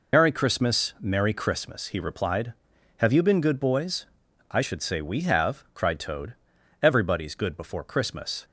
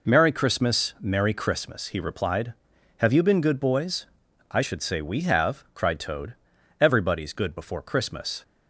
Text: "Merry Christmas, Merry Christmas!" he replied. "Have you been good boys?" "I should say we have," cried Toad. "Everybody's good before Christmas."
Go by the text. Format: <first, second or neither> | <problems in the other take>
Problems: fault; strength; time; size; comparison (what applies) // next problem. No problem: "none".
second | loses the start of "Merry"; at 0.1 s; 80 ms